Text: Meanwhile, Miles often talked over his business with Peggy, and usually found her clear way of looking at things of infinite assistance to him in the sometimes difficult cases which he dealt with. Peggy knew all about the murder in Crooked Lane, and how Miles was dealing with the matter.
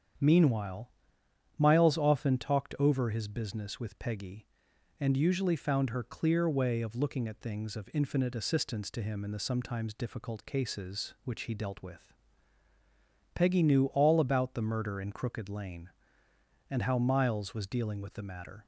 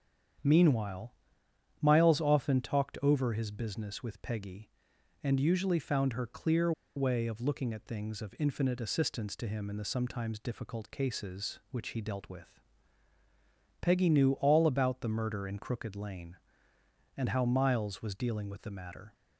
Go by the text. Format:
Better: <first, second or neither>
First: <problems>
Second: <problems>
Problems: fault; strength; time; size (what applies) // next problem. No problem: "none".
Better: first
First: starts louder than the rest; strong; until 1.8 s; 8.5 dB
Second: starts louder than the rest; strong; until 2.1 s; 8.5 dB // pauses between "clear" and "way"; slight; at 6.7 s; 0.24 s long